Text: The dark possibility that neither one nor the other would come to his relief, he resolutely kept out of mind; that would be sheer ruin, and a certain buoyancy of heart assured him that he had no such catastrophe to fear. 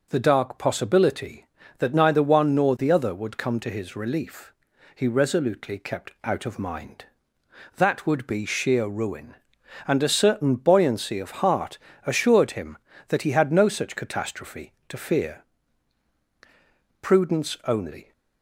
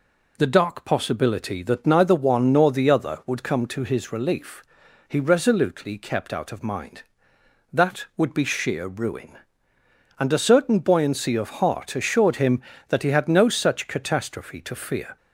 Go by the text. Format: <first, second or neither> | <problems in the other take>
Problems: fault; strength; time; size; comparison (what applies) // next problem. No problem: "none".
second | pauses between "heart" and "assured"; slight; at 11.7 s; 0.30 s long // goes on to say "Prudence only"; noticeable; from 17.0 s on; 1.1 s long